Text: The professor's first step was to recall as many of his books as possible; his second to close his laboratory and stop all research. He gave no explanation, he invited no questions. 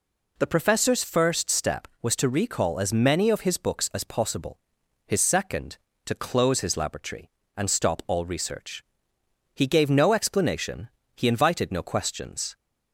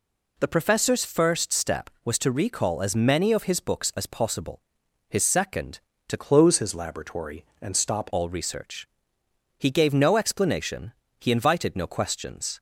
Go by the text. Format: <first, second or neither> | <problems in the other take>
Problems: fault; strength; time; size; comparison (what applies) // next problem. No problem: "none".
first | changes voice from "close" to "stop"; from 6.1 to 8.0 s; 1.9 s long